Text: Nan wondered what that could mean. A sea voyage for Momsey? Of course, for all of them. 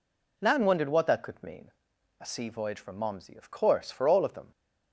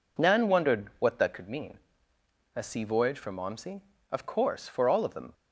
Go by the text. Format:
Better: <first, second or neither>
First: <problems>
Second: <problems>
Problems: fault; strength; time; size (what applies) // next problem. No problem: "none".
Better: neither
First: none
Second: none